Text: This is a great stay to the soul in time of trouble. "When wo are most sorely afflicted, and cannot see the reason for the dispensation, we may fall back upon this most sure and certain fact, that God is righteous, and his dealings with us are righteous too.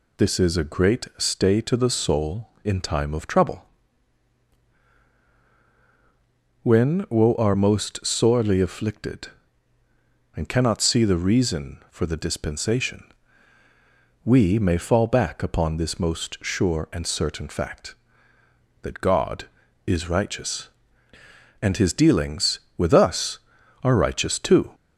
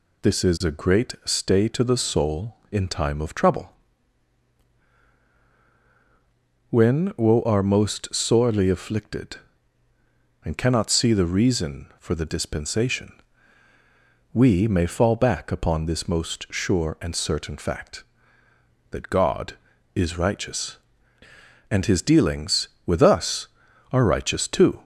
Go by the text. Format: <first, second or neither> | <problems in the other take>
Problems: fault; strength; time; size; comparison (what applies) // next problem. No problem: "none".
neither | none